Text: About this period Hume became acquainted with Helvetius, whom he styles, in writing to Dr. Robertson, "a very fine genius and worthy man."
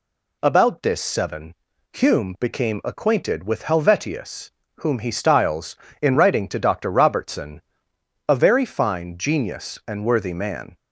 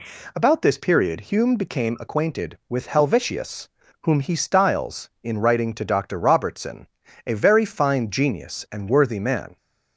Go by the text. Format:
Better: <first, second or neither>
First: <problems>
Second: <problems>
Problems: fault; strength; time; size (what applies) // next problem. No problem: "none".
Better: second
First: says "seven" for "period"; at 1.0 s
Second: none